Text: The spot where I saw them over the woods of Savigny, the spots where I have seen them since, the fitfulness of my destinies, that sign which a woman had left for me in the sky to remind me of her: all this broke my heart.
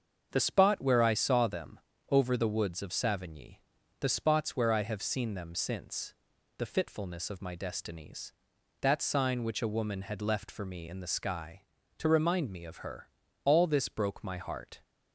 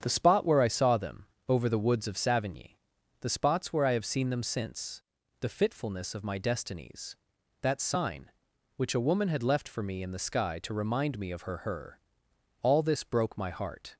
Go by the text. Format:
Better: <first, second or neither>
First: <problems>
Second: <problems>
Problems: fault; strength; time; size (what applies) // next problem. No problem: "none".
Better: first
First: starts louder than the rest; until 1.3 s; 7 dB // pauses between "them" and "over"; slight; at 1.7 s; 0.28 s long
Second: starts louder than the rest; strong; until 1.0 s; 8 dB // pauses between "them" and "over"; slight; at 1.2 s; 0.22 s long // says "her" twice; at 11.5 s